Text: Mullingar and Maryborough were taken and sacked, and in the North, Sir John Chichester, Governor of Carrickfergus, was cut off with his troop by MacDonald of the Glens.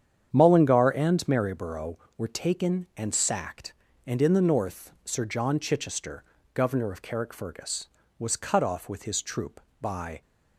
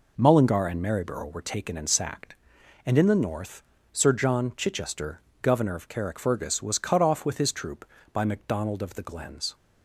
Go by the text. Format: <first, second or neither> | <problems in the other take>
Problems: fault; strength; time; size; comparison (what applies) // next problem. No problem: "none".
second | starts louder than the rest; strong; until 1.3 s; 8.5 dB // stops before "MacDonald of the Glens"; at 10.2 s